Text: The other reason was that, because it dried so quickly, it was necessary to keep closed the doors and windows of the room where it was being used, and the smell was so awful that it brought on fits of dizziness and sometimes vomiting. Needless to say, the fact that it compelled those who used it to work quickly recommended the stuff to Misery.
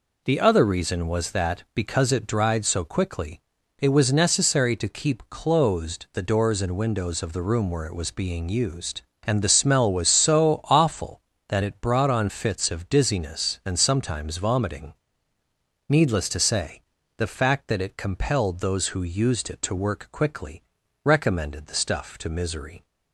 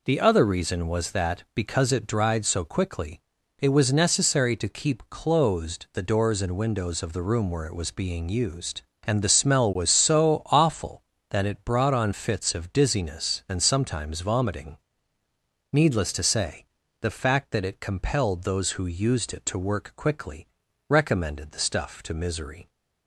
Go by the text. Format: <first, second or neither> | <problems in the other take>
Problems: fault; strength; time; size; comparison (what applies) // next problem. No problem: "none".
neither | pauses between "quickly" and "recommended"; the same in both